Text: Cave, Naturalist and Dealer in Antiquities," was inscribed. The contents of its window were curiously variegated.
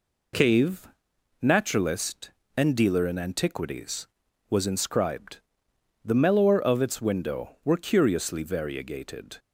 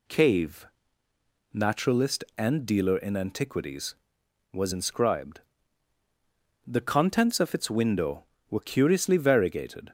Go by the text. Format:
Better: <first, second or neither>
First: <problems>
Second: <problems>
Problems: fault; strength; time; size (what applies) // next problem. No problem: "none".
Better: second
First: says "mellower" for "contents"; at 6.1 s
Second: none